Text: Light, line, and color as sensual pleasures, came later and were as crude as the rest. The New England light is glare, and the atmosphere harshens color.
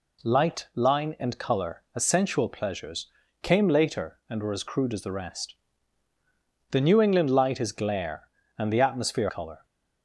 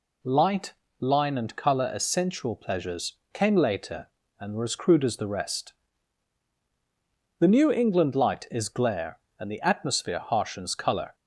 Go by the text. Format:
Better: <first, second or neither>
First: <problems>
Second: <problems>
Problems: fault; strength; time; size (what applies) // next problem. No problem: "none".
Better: second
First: skips "harshens"; at 9.2 s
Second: none